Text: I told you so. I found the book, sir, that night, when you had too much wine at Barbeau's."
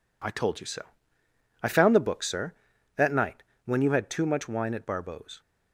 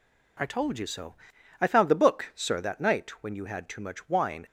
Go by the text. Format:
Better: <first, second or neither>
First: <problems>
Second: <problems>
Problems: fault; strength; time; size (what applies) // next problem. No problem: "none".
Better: first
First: none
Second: stops before "at Barbeau's"; at 4.4 s